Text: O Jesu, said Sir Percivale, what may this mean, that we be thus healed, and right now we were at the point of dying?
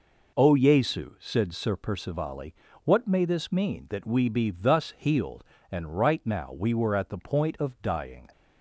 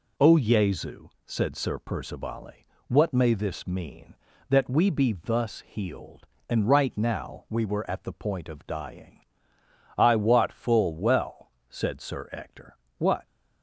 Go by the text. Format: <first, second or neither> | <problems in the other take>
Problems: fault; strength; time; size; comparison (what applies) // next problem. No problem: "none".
first | goes on to say "I wot full well said Sir Ector what"; strong; from 9.9 s on; 3.2 s long